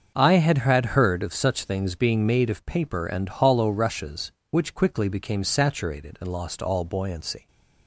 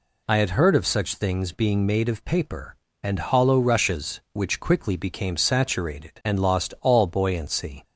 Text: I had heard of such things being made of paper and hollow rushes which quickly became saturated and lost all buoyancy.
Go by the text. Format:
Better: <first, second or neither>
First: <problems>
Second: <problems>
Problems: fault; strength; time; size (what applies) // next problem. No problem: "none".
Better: second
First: starts louder than the rest; until 1.1 s; 6.5 dB // says "had" twice; at 0.5 s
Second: none